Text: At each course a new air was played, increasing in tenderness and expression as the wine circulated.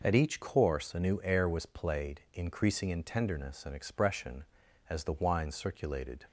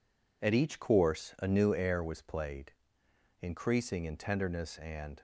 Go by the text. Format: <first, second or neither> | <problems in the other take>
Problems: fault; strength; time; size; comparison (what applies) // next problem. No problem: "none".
first | stops before "expression as the wine circulated"; at 5.1 s